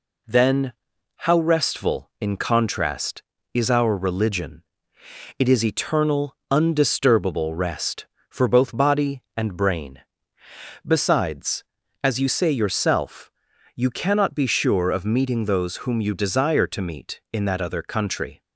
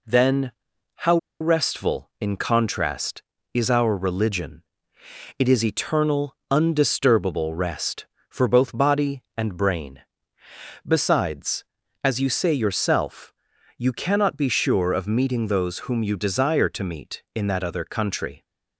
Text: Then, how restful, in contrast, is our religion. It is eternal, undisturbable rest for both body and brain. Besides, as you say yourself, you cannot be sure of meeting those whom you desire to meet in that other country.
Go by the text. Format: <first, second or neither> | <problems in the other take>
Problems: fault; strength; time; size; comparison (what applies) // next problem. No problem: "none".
first | pauses between "how" and "restful"; slight; at 1.1 s; 0.23 s long